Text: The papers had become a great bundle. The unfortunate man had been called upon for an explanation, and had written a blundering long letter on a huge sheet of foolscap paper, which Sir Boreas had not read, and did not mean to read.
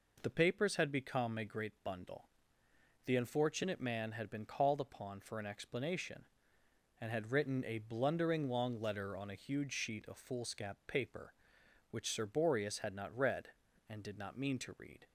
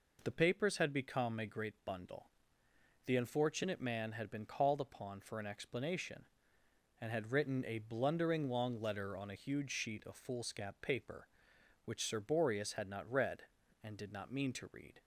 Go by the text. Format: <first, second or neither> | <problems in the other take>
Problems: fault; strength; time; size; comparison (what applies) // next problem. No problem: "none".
neither | none